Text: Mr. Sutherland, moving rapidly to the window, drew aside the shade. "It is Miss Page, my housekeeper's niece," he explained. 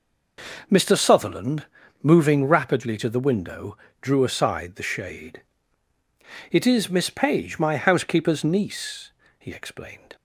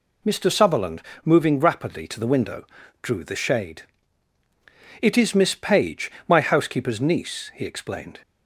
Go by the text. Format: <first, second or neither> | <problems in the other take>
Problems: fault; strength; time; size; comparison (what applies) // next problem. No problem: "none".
first | skips "aside"; at 3.2 s